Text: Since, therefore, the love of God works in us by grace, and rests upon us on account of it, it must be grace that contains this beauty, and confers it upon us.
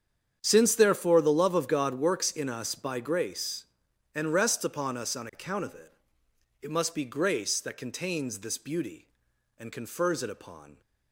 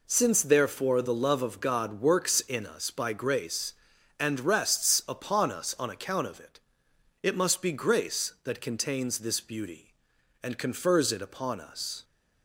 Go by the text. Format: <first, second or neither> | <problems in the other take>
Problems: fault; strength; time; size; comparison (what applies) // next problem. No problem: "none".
second | starts louder than the rest; strong; until 1.4 s; 8 dB // stops before "us"; at 10.8 s